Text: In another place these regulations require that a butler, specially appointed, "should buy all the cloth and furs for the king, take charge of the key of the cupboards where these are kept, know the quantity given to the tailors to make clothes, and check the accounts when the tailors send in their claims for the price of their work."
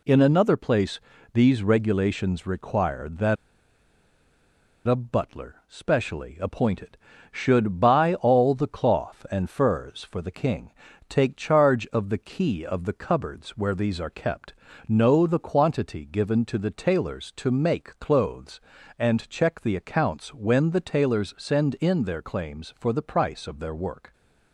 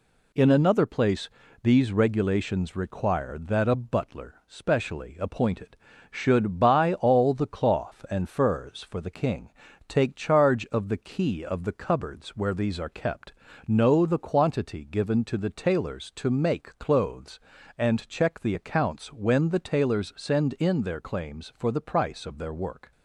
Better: second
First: pauses between "place" and "these"; slight; at 0.9 s; 0.34 s long // pauses between "that" and "a"; strong; at 3.3 s; 1.5 s long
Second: pauses between "place" and "these"; slight; at 1.2 s; 0.34 s long

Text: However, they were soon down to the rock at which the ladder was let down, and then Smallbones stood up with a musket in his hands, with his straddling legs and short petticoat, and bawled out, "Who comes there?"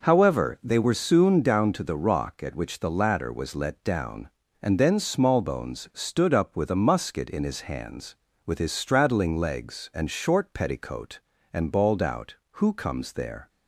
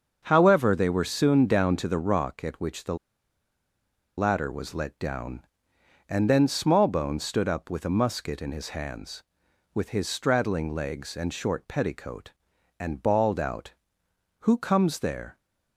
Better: first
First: none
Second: starts louder than the rest; until 1.2 s; 6.5 dB // pauses between "the" and "ladder"; at 2.9 s; 1.2 s long

